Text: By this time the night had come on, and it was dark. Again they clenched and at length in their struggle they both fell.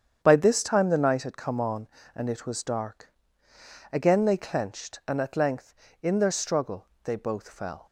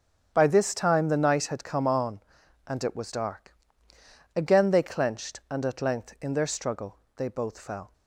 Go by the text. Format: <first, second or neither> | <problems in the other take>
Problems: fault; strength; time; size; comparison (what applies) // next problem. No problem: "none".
neither | starts louder than the rest; strong; the same in both // pauses between "struggle" and "they"; slight; the same in both